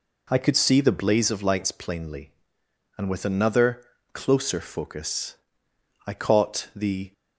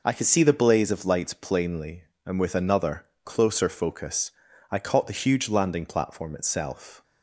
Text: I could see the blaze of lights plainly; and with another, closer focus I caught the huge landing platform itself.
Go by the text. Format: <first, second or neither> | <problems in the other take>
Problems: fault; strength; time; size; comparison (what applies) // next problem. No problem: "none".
second | pauses between "focus" and "I"; noticeable; at 5.3 s; 0.70 s long; also in the second // stops before "huge landing platform itself"; at 7.1 s